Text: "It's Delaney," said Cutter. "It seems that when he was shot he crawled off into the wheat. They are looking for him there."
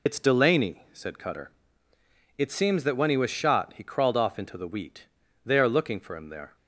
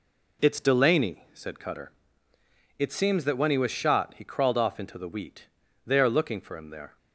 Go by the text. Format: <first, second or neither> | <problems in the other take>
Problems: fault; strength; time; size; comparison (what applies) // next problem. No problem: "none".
second | loses the start of "It's"; at 0.0 s; 60 ms